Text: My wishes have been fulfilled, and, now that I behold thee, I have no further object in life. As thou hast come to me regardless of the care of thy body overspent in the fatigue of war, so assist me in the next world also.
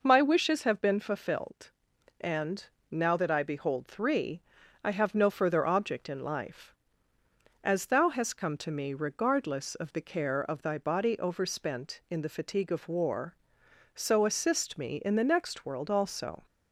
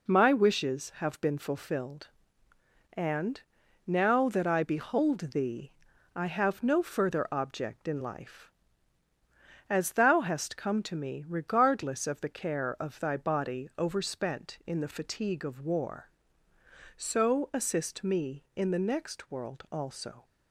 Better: second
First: says "three" for "thee"; at 3.8 s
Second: none

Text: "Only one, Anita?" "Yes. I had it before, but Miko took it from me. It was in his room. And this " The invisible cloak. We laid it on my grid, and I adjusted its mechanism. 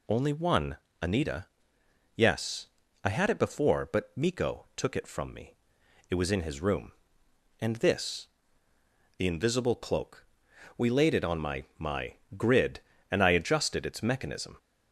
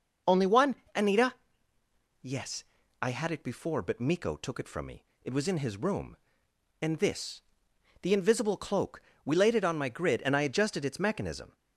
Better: second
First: says "my" twice; at 11.7 s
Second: none

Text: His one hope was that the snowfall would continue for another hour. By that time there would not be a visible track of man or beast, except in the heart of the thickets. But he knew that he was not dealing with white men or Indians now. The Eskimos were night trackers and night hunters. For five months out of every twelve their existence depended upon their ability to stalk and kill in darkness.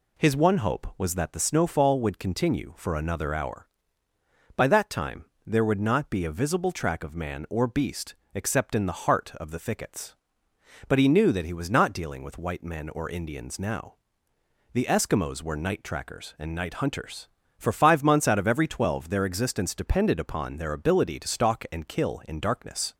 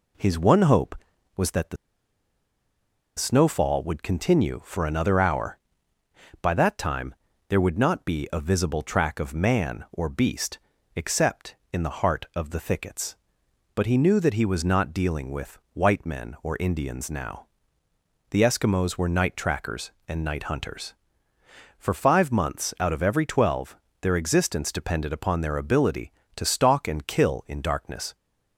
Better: first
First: pauses between "time" and "there"; slight; at 5.2 s; 0.20 s long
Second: pauses between "the" and "snowfall"; strong; at 1.7 s; 1.4 s long // pauses between "time" and "there"; slight; at 7.1 s; 0.34 s long // pauses between "twelve" and "their"; slight; at 23.7 s; 0.26 s long

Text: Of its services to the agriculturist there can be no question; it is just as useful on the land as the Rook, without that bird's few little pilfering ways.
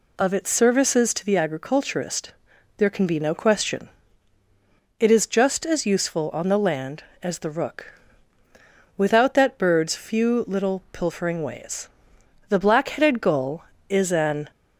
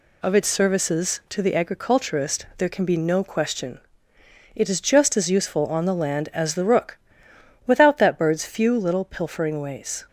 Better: second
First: pauses between "agriculturist" and "there"; at 2.3 s; 0.44 s long // goes on to say "The Black headed Gull is an"; strong; from 12.5 s on; 2.0 s long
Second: none

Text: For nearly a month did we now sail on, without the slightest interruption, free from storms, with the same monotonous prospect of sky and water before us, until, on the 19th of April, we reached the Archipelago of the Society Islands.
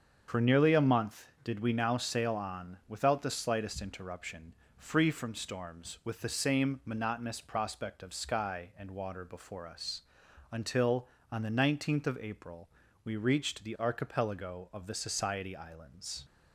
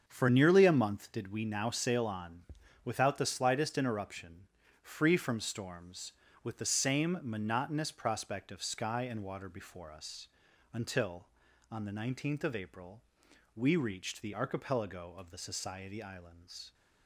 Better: neither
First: starts louder than the rest; until 1.2 s; 7 dB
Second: starts louder than the rest; until 1.0 s; 7 dB

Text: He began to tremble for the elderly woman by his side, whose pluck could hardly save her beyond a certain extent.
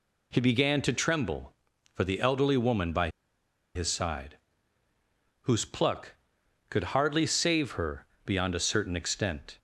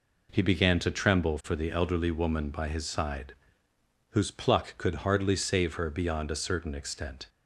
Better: second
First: pauses between "by" and "his"; noticeable; at 3.0 s; 0.65 s long // pauses between "her" and "beyond"; slight; at 8.0 s; 0.18 s long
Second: none

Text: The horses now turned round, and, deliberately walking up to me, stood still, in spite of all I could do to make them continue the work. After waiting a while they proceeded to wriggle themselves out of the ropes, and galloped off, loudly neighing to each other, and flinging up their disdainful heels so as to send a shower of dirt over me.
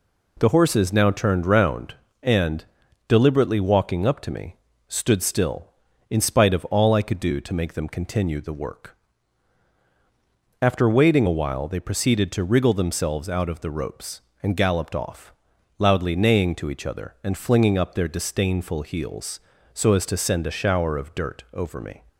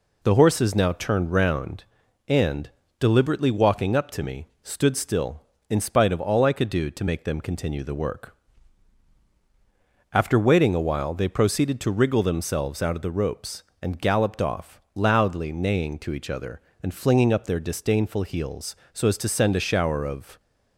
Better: first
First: none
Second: stops before "dirt over me"; at 20.4 s

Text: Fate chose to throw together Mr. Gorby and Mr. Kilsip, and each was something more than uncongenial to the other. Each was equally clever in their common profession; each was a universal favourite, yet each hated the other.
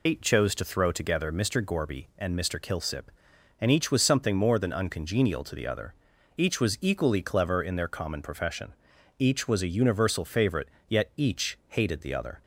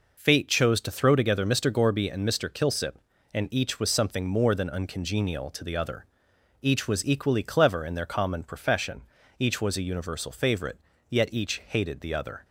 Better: second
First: loses the start of "Fate"; at 0.0 s; 100 ms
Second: none

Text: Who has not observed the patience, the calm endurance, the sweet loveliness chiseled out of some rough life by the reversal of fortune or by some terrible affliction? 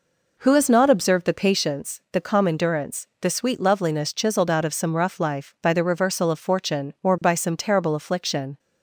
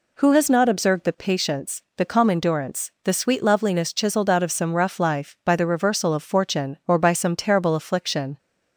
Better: second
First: starts louder than the rest; noticeable; until 1.7 s; 4.5 dB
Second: none

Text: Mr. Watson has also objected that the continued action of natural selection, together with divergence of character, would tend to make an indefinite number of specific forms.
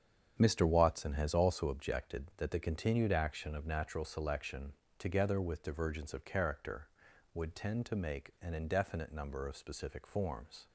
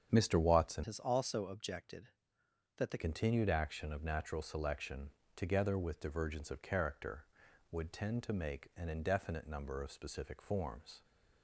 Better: first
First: starts louder than the rest; strong; until 1.4 s; 8 dB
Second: starts louder than the rest; strong; until 1.1 s; 8 dB // changes voice from "has" to "the"; from 0.8 to 2.9 s; 2.1 s long

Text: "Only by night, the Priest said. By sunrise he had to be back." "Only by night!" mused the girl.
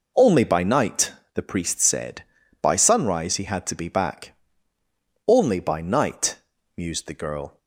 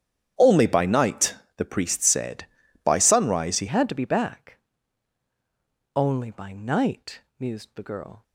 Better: first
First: none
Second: starts louder than the rest; strong; until 1.6 s; 9.5 dB // changes voice at "had"; from 3.6 s on; 4.6 s long

